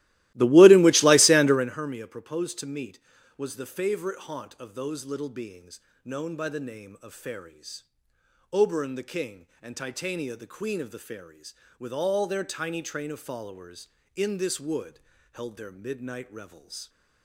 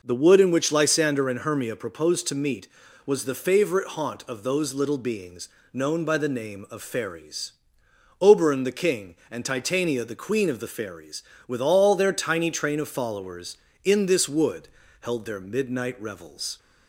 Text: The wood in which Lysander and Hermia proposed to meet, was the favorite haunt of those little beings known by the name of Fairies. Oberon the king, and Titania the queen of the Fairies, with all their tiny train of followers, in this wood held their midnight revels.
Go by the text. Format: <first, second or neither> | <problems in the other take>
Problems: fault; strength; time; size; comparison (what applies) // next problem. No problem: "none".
second | starts louder than the rest; strong; until 1.8 s; 17 dB // pauses between "beings" and "known"; slight; at 5.7 s; 0.24 s long; slight in the second // pauses between "wood" and "held"; slight; at 14.9 s; 0.34 s long; slight in the second